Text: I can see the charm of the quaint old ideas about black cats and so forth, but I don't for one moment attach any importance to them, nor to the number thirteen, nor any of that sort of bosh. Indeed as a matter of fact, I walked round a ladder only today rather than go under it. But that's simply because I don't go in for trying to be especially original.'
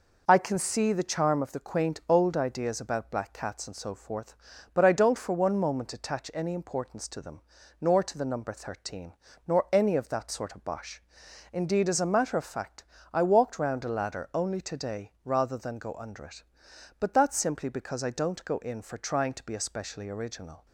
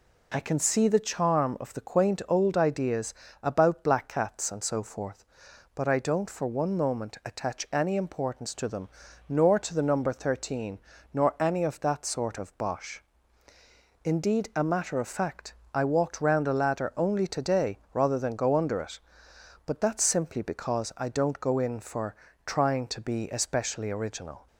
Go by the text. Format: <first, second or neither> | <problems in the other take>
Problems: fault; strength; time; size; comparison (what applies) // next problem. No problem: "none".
first | pauses between "ideas" and "about"; slight; at 3.1 s; 0.30 s long // skips "as"; at 14.5 s // pauses between "today" and "rather"; slight; at 17.7 s; 0.16 s long // pauses between "for" and "trying"; slight; at 22.1 s; 0.32 s long